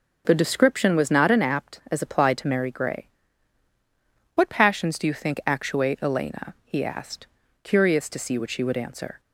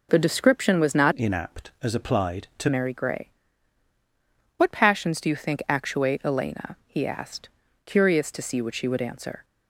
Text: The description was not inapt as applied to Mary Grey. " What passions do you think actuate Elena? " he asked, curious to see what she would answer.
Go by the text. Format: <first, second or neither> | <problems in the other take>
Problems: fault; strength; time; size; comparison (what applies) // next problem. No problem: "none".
first | changes voice from "inapt" to "to"; from 1.1 to 2.6 s; 1.5 s long